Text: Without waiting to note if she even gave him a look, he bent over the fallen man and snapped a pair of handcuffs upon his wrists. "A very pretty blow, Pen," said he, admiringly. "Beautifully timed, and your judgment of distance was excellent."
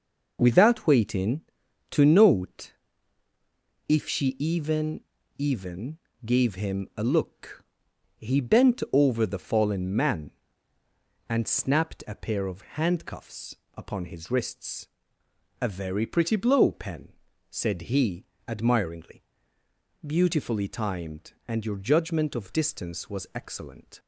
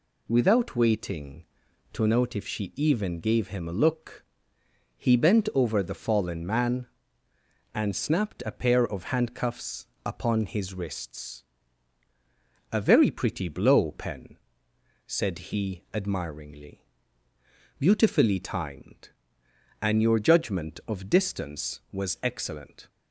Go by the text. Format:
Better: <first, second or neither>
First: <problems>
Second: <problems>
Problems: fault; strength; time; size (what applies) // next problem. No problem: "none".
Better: second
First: pauses between "note" and "if"; at 2.7 s; 1.1 s long // says "even" twice; at 5.3 s // pauses between "handcuffs" and "upon"; slight; at 13.5 s; 0.20 s long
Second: pauses between "handcuffs" and "upon"; slight; at 9.8 s; 0.20 s long